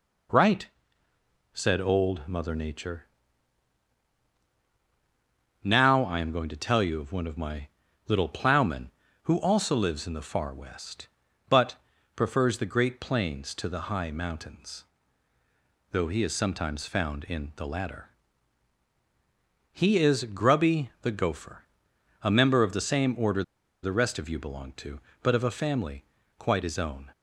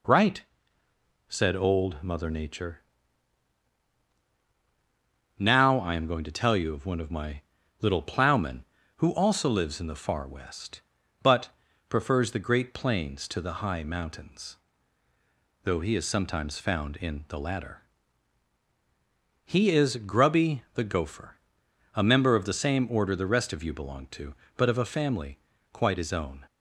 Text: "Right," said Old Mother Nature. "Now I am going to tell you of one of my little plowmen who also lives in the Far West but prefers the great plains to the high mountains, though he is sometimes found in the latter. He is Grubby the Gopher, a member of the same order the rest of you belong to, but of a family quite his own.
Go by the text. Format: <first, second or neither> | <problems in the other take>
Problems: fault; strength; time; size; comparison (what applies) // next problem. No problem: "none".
second | pauses between "my" and "little"; at 7.6 s; 0.40 s long; also in the second // pauses between "but" and "prefers"; at 11.7 s; 0.40 s long; also in the second // pauses between "order" and "the"; at 23.4 s; 0.40 s long // pauses between "family" and "quite"; slight; at 26.0 s; 0.32 s long; slight in the second